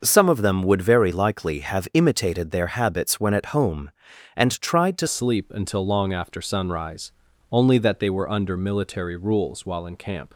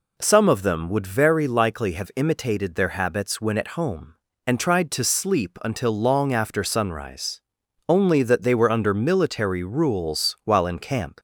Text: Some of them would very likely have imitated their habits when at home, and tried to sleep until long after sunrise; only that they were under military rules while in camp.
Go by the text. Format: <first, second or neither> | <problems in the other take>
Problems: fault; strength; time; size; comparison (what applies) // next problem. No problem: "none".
second | starts louder than the rest; noticeable; until 1.0 s; 6 dB // changes voice at "sleep"; from 5.0 s on; 5.3 s long